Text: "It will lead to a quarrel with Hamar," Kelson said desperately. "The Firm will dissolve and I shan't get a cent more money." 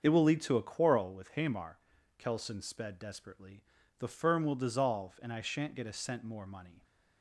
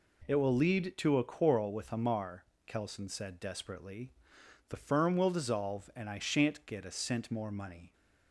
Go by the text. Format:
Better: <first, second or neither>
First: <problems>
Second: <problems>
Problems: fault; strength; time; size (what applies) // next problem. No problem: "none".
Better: second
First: starts louder than the rest; until 1.0 s; 6.5 dB // says "sped" for "said"; at 2.6 s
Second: none